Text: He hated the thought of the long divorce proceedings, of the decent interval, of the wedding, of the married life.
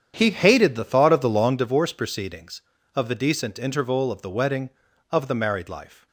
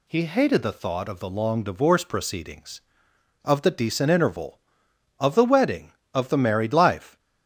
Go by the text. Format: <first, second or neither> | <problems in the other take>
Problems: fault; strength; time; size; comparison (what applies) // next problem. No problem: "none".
second | starts louder than the rest; strong; until 1.6 s; 8.5 dB